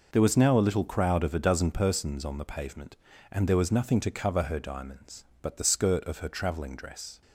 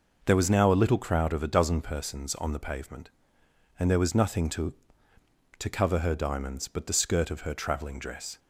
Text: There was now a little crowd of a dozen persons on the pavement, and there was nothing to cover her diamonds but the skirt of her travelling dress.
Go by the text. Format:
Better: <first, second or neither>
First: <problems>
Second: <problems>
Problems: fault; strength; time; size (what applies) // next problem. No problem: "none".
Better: first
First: none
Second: says "to" twice; at 5.5 s